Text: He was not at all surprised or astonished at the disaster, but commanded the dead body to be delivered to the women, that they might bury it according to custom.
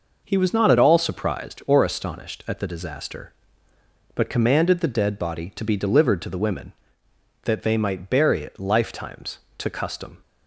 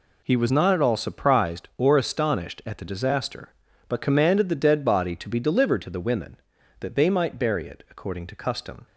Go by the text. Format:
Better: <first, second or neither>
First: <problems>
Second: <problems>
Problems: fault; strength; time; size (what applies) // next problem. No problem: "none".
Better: second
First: says "lifetimes" for "according"; at 8.5 s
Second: none